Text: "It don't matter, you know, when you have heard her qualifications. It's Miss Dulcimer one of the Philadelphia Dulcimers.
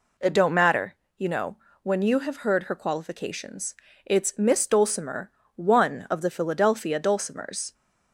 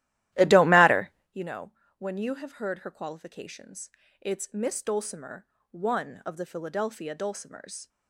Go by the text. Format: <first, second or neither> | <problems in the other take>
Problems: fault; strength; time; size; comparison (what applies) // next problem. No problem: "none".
first | starts louder than the rest; strong; until 1.4 s; 14.5 dB // pauses between "Dulcimer" and "one"; slight; at 5.4 s; 0.24 s long; slight in the first